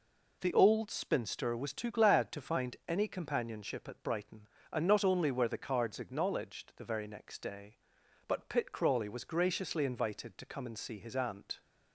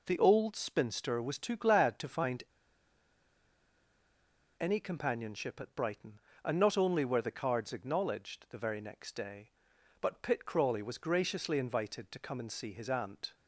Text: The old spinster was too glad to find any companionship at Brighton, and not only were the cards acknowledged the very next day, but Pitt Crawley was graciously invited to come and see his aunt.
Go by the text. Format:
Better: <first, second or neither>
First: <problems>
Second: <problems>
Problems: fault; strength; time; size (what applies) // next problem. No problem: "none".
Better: first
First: none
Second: pauses between "find" and "any"; strong; at 2.4 s; 2.1 s long